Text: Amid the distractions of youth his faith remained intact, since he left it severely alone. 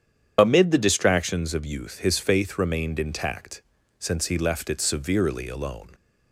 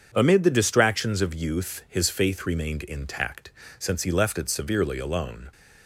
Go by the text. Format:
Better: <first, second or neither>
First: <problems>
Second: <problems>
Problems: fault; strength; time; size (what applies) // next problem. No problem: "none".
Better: second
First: loses the start of "Amid"; at 0.3 s; 35 ms // starts louder than the rest; strong; until 1.3 s; 8.5 dB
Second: starts louder than the rest; strong; until 1.1 s; 7.5 dB